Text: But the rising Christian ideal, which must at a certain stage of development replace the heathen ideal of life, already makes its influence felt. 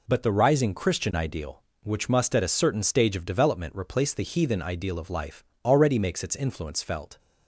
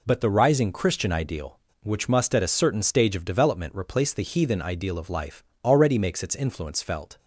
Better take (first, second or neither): neither